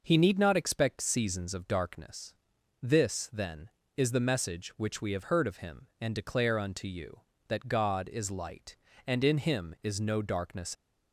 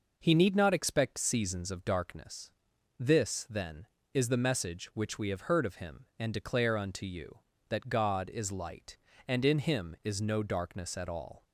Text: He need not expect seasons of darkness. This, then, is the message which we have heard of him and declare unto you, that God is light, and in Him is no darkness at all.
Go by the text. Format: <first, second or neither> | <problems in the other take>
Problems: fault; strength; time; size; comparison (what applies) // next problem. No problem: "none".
second | stops before "at all"; at 10.7 s